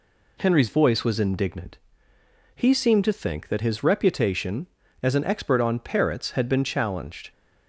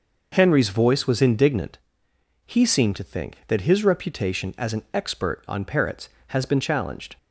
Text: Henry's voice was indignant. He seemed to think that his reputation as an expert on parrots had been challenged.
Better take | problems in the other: first | says "has" for "had"; at 6.2 s

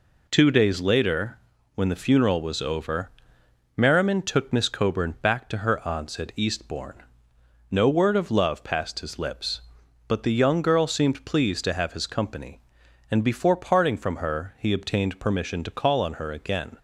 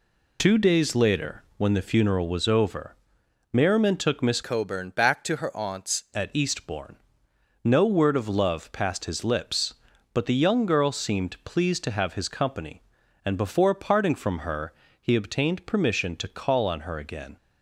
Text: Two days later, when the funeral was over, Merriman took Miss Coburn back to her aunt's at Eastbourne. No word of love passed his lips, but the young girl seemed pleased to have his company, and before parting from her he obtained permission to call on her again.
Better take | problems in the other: first | changes voice from "Coburn" to "aunt's"; from 4.4 to 6.0 s; 1.6 s long // pauses between "her" and "he"; slight; at 14.7 s; 0.26 s long

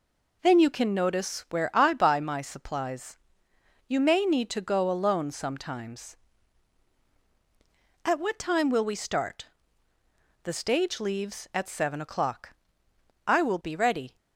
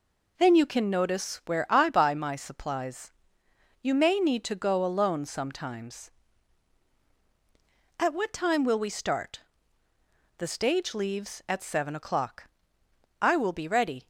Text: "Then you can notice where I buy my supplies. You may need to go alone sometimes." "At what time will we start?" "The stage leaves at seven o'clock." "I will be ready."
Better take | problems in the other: neither | none

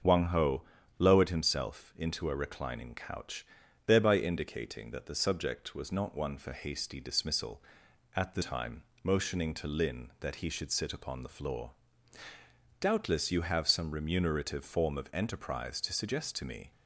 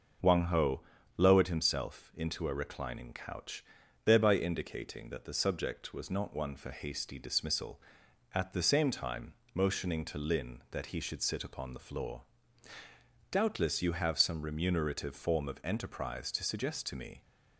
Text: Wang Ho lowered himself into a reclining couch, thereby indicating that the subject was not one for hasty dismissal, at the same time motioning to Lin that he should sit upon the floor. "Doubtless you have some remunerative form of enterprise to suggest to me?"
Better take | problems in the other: second | starts louder than the rest; until 1.4 s; 6.5 dB // pauses between "Ho" and "lowered"; slight; at 0.6 s; 0.36 s long; slight in the second // skips "same"; at 8.4 s // pauses between "time" and "motioning"; slight; at 8.8 s; 0.20 s long; slight in the second

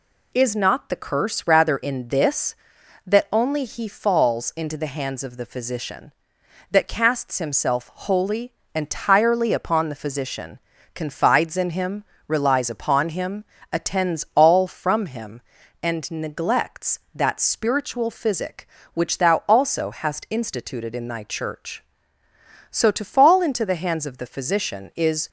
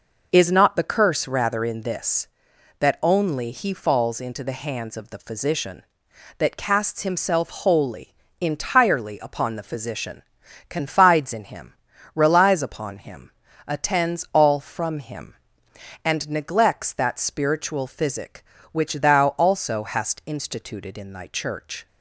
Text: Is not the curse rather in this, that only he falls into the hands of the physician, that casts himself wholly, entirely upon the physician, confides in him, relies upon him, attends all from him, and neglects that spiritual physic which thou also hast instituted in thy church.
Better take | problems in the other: second | goes on to say "So to fall into the hands of the physician is"; strong; from 22.7 s on; 2.5 s long

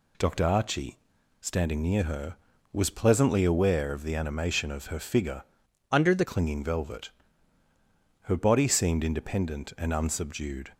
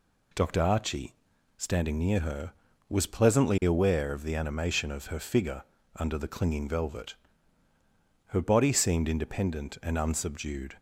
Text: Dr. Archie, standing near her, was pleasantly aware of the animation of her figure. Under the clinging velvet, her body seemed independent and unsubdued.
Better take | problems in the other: second | changes voice from "Under" to "the"; from 5.9 to 6.2 s; 0.3 s long

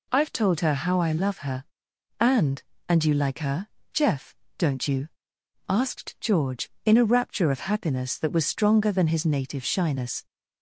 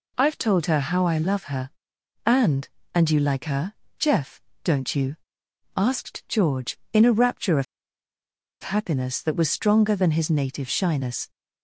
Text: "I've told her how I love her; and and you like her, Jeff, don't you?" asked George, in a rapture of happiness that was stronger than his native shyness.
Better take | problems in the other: first | pauses between "of" and "happiness"; at 7.6 s; 0.99 s long

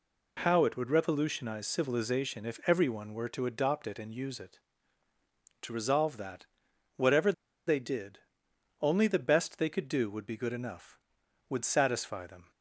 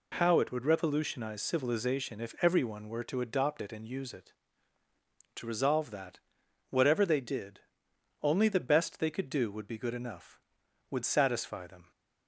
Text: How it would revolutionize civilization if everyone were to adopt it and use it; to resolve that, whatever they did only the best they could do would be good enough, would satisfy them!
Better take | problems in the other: second | pauses between "whatever" and "they"; slight; at 7.3 s; 0.35 s long // pauses between "did" and "only"; noticeable; at 8.1 s; 0.62 s long; noticeable in the second

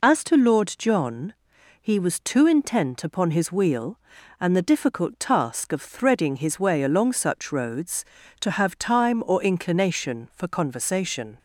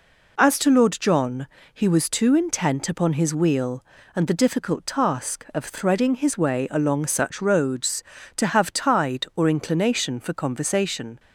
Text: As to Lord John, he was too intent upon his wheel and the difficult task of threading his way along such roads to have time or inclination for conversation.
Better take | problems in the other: first | says "tide" for "time"; at 8.7 s

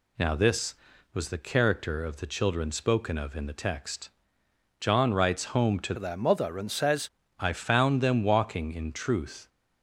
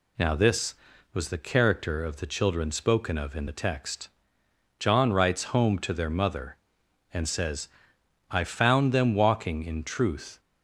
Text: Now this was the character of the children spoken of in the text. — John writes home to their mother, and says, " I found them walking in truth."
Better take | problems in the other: second | changes voice from "their" to "says"; from 5.9 to 7.0 s; 1.1 s long

